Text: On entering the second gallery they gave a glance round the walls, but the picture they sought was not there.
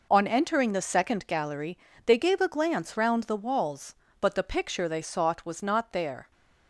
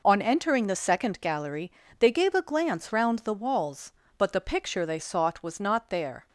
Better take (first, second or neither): neither